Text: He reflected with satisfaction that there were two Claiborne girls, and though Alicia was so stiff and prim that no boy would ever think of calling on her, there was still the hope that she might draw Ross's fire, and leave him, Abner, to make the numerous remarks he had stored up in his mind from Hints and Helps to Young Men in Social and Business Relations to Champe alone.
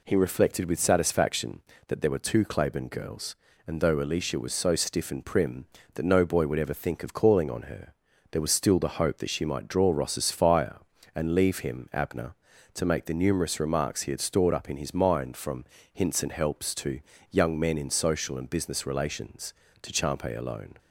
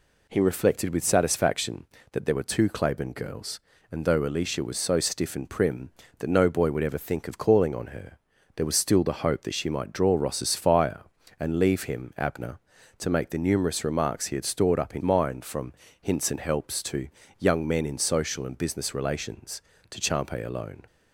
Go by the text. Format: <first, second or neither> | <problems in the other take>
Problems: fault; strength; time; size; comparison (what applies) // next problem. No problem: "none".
first | skips "his"; at 15.0 s // pauses between "from" and "Hints"; slight; at 15.7 s; 0.26 s long; slight in the first // pauses between "to" and "Young"; slight; at 17.0 s; 0.30 s long; slight in the first